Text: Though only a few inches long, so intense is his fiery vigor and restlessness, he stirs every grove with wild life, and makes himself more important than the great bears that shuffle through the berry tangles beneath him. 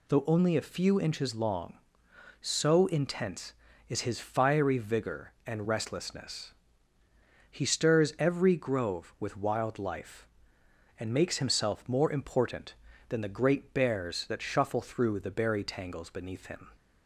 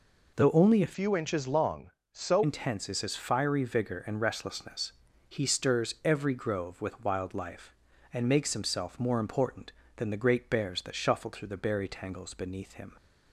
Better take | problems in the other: first | changes voice from "few" to "so"; from 0.9 to 2.4 s; 1.5 s long

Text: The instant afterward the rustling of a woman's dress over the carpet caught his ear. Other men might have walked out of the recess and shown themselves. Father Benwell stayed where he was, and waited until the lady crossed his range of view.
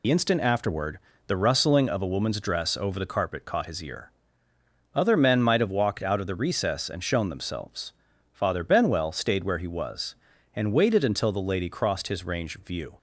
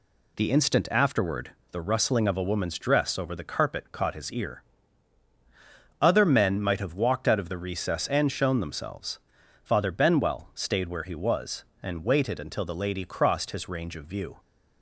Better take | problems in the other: second | loses the start of "The"; at 0.0 s; 65 ms // pauses between "afterward" and "the"; slight; at 0.9 s; 0.28 s long; slight in the second

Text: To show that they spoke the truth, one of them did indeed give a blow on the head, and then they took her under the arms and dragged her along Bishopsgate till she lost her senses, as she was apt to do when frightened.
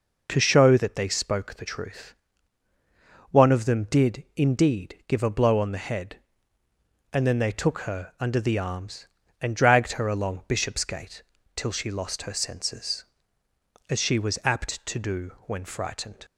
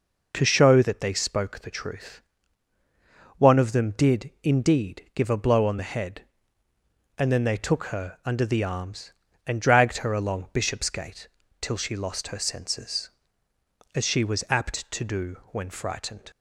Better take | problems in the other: neither | pauses between "Bishopsgate" and "till"; slight; the same in both

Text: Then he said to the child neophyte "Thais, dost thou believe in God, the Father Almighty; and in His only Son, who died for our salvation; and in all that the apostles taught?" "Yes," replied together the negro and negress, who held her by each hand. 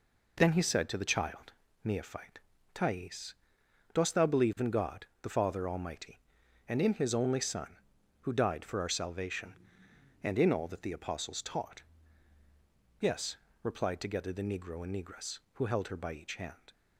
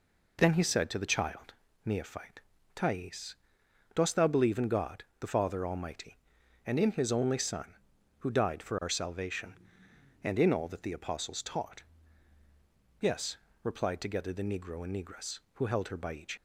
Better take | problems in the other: first | pauses between "child" and "neophyte"; slight; at 1.5 s; 0.32 s long; slight in the first // pauses between "neophyte" and "Thais"; slight; at 2.3 s; 0.34 s long; slight in the first // stops before "hand"; at 16.3 s

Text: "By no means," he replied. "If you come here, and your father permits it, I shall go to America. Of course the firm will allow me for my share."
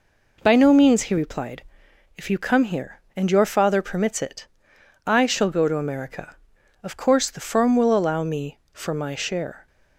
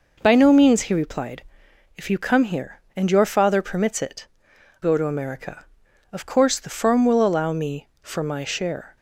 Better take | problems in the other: first | skips "I shall"; at 4.5 s

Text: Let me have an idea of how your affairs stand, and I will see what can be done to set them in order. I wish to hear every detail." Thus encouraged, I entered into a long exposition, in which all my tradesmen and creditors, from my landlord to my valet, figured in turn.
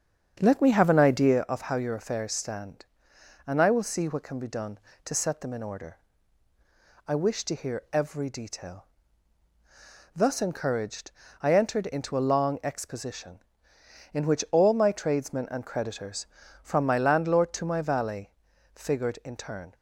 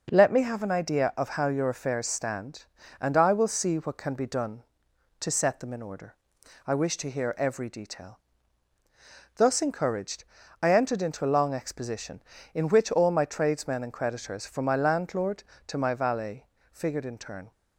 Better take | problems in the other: second | starts louder than the rest; strong; until 1.4 s; 7.5 dB

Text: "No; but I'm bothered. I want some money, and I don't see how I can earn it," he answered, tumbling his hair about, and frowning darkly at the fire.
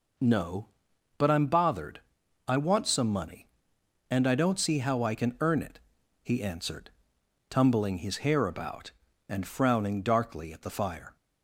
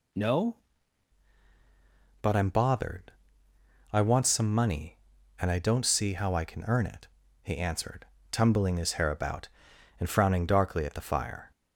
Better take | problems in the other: first | changes voice at "but"; from 2.2 s on; 9.3 s long

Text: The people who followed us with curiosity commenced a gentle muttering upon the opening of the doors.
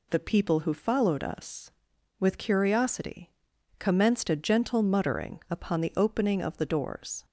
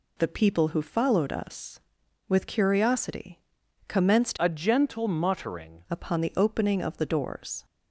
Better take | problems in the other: first | pauses between "curiosity" and "commenced"; noticeable; at 3.3 s; 0.48 s long; noticeable in the first // changes voice from "a" to "muttering"; from 4.3 to 5.8 s; 1.5 s long

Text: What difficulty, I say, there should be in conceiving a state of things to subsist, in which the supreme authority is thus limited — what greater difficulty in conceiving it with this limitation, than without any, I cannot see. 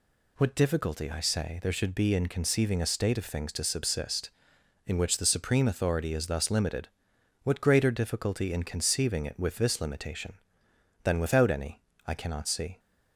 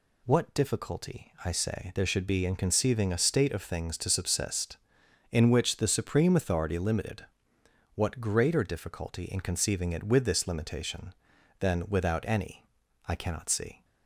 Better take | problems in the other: first | skips "is thus"; at 6.7 s

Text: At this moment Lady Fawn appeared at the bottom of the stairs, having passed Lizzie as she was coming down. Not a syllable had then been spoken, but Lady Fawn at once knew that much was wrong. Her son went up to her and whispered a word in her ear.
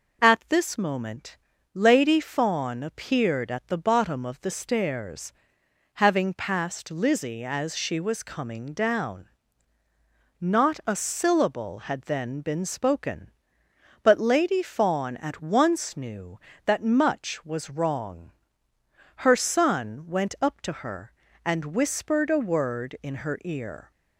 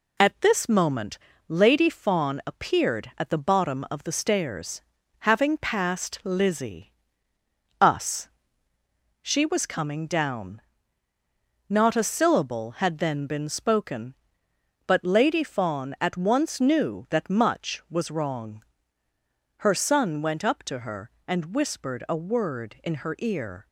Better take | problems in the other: first | pauses between "moment" and "Lady"; slight; at 1.1 s; 0.28 s long; slight in the first // says "us" for "as"; at 7.7 s

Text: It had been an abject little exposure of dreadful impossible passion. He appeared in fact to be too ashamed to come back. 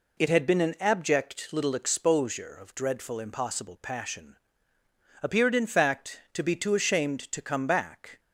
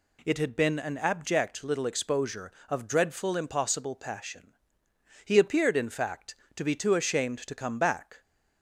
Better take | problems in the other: second | skips "He"; at 4.7 s

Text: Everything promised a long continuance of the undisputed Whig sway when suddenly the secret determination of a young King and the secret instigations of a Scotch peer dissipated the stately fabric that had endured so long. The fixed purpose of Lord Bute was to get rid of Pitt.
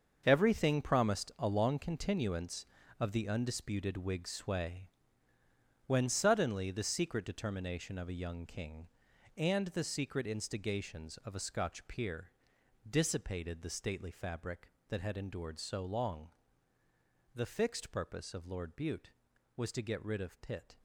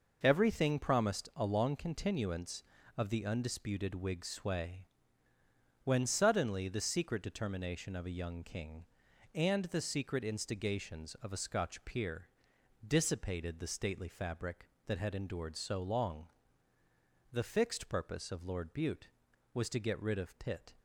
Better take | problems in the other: second | gets quieter; strong; throughout; 11 dB // pauses between "sway" and "when"; noticeable; at 4.8 s; 0.98 s long; noticeable in the second // pauses between "peer" and "dissipated"; noticeable; at 12.3 s; 0.58 s long; noticeable in the second

